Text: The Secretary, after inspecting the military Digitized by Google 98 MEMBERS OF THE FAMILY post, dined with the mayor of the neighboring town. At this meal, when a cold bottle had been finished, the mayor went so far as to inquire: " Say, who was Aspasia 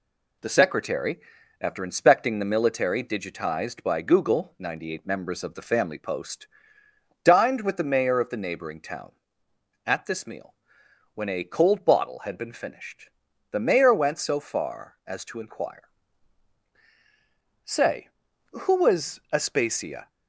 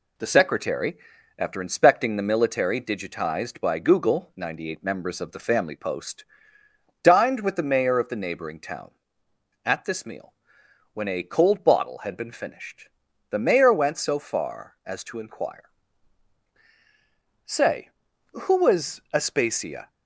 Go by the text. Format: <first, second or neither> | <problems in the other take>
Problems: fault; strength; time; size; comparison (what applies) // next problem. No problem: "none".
neither | none